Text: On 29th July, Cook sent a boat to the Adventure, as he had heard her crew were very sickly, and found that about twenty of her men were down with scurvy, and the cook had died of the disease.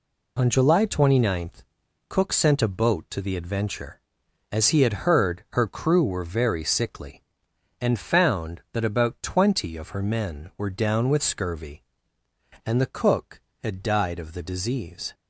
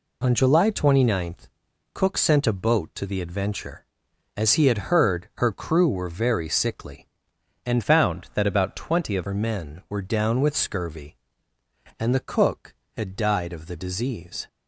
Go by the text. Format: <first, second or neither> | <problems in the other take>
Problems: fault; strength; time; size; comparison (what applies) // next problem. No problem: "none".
first | changes voice from "found" to "of"; from 7.8 to 9.2 s; 1.4 s long